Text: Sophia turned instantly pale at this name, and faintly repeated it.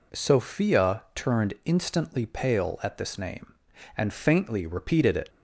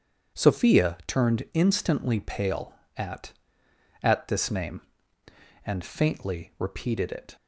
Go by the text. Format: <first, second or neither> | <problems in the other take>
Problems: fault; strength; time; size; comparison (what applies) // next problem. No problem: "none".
first | says "at" twice; at 4.0 s